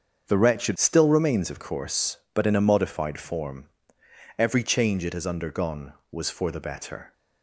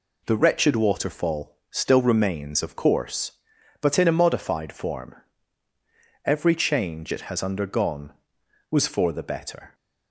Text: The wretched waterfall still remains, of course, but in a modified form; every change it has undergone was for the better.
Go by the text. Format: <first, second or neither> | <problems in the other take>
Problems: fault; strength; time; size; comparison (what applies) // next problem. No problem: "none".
second | starts louder than the rest; strong; until 1.2 s; 7 dB // skips "waterfall"; at 0.7 s